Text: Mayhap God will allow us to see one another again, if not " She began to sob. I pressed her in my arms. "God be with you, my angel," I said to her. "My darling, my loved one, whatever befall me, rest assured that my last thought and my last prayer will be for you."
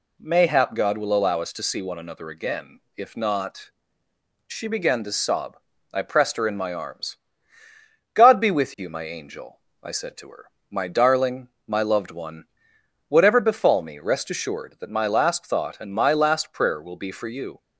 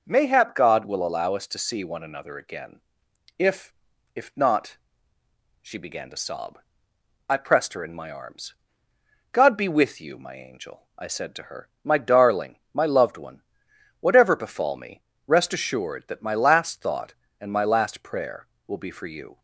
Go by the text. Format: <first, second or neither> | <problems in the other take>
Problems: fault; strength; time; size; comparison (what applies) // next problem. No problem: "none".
first | says "if" twice; at 4.1 s